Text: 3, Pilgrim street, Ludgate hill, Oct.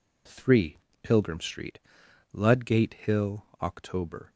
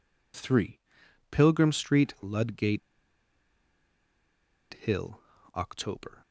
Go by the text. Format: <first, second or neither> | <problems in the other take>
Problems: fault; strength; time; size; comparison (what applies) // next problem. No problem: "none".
first | pauses between "Ludgate" and "hill"; strong; at 2.8 s; 1.9 s long